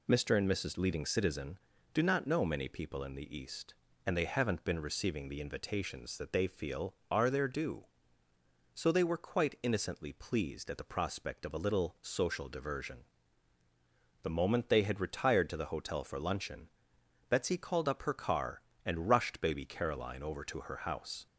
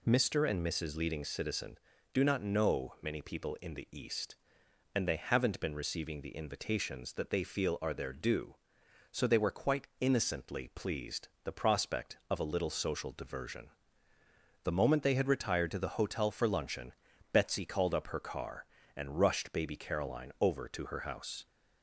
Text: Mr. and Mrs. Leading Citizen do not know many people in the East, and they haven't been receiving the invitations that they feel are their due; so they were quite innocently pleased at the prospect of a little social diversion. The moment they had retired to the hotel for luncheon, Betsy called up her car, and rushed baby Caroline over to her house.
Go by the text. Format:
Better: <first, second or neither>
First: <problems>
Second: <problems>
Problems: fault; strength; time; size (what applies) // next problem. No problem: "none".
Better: first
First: none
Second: skips "at"; at 11.3 s